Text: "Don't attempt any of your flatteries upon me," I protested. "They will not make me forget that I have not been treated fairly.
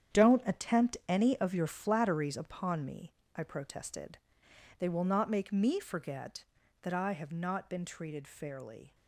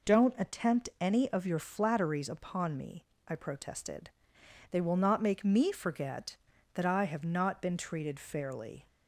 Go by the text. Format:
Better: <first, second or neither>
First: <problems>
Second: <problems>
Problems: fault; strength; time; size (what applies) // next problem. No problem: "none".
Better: second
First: gets quieter; strong; throughout; 10.5 dB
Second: none